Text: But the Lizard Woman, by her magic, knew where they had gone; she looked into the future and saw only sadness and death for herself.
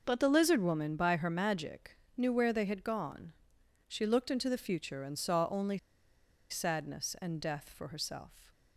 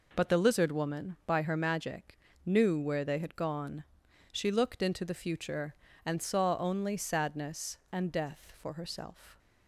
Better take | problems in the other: second | pauses between "only" and "sadness"; noticeable; at 5.7 s; 0.72 s long

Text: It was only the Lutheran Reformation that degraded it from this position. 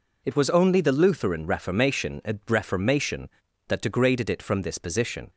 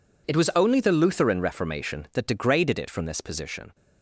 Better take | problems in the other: second | says "Reformation" twice; at 2.4 s

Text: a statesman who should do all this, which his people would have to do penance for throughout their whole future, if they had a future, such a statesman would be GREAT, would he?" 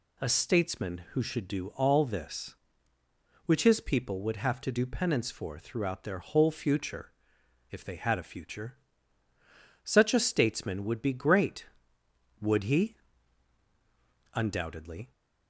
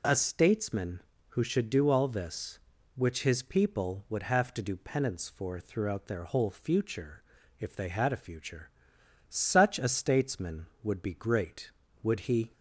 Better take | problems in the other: second | goes on to say "Undoubtedly"; noticeable; from 14.3 s on; 0.78 s long

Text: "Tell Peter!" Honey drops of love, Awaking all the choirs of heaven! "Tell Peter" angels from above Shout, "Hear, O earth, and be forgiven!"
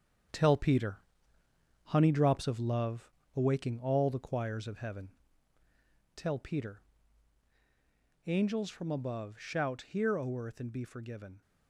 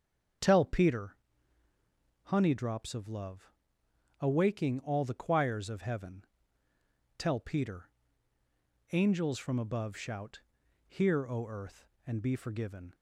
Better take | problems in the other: second | gets quieter; strong; throughout; 7.5 dB // starts louder than the rest; strong; until 2.1 s; 7.5 dB; strong in the second // pauses between "Peter" and "angels"; strong; at 6.8 s; 1.4 s long; also in the second

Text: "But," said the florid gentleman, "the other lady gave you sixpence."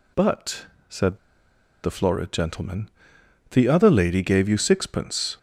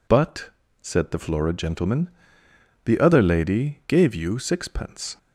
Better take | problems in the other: second | pauses between "said" and "the"; noticeable; at 1.1 s; 0.65 s long

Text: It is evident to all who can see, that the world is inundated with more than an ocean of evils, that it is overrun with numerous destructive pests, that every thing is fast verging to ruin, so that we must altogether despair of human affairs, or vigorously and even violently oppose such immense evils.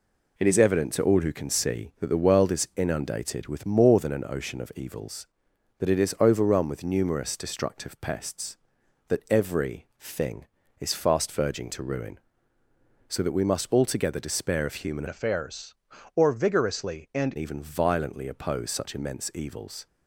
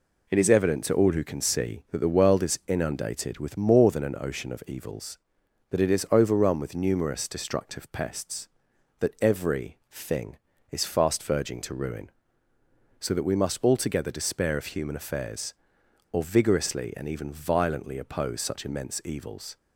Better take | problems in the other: second | changes voice from "affairs" to "and"; from 15.0 to 17.3 s; 2.3 s long

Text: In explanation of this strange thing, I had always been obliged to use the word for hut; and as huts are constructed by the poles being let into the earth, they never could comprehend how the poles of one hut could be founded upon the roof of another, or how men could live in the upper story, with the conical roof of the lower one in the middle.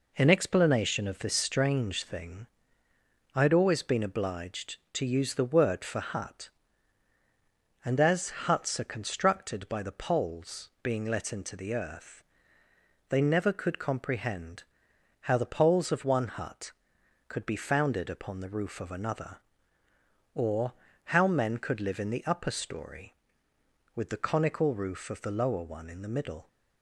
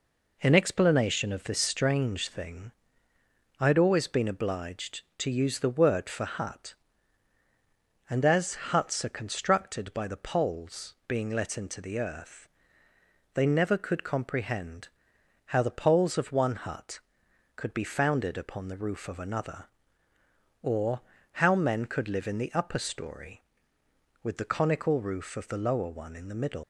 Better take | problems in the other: first | pauses between "comprehend" and "how"; noticeable; at 14.8 s; 0.56 s long; noticeable in the first // pauses between "or" and "how"; at 20.9 s; 0.42 s long; also in the first // leaves "middle" unfinished; at 26.6 s; 110 ms

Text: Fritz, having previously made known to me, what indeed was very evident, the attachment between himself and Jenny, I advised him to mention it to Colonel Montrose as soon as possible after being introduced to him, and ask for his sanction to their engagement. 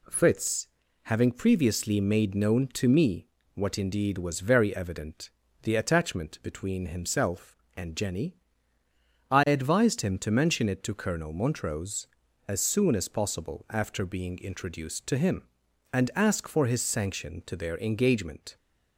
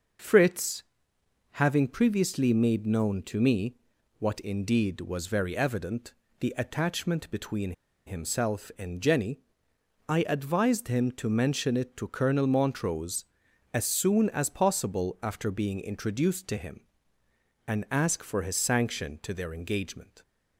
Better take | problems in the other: first | pauses between "between" and "himself"; slight; at 7.7 s; 0.34 s long

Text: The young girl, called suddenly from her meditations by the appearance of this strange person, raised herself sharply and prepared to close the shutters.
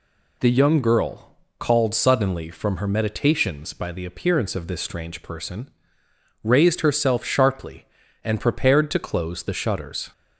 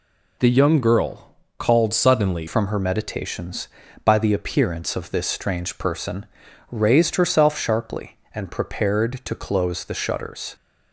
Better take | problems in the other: first | changes voice at "from"; from 2.4 s on; 8.1 s long

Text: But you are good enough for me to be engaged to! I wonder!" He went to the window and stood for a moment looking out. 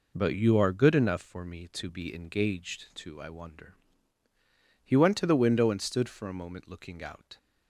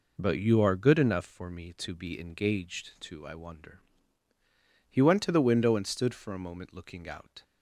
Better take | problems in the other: neither | none

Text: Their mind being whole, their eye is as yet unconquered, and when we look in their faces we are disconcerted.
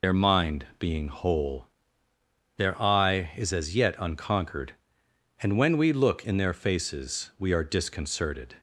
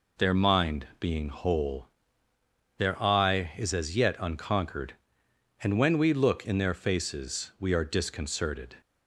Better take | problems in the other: second | loses the start of "Their"; at 0.0 s; 55 ms

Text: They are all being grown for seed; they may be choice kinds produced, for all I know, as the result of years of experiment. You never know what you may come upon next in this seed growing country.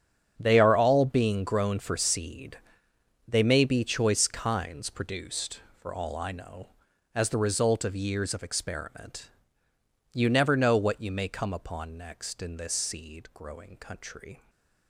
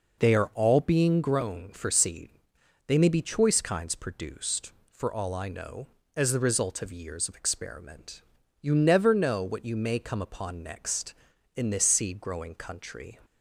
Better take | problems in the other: second | gets quieter; strong; throughout; 14 dB

